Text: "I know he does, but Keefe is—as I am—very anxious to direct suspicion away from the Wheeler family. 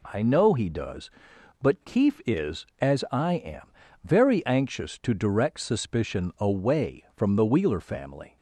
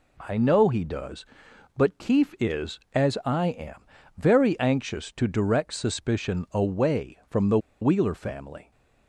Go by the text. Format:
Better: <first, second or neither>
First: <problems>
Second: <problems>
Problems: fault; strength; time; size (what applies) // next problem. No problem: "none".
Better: first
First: none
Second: pauses between "the" and "Wheeler"; slight; at 7.5 s; 0.23 s long